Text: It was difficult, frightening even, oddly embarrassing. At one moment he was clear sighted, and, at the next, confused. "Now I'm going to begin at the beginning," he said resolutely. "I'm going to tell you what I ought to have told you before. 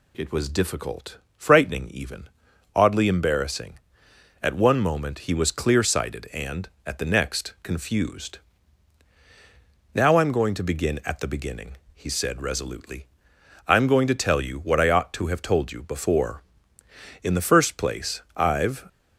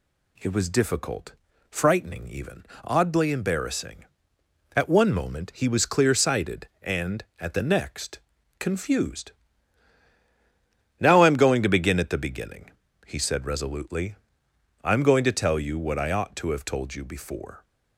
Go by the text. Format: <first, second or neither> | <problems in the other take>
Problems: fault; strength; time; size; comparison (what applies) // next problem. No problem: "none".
second | goes on to say "In the first place I've"; from 17.2 s on; 1.6 s long